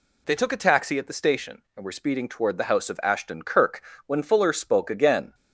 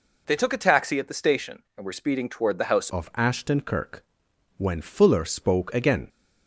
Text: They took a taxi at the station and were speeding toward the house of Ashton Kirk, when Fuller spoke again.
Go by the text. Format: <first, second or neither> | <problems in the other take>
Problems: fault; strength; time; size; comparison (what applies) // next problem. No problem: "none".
first | changes voice at "of"; from 2.8 s on; 3.2 s long